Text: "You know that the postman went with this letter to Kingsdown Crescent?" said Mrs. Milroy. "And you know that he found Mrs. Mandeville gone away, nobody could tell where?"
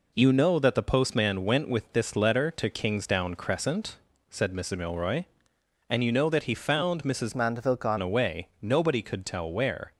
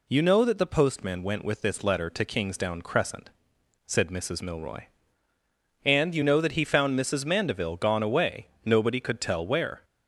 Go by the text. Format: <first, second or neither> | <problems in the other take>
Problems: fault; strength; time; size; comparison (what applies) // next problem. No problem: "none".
second | changes voice from "Mandeville" to "gone"; from 7.3 to 7.9 s; 0.6 s long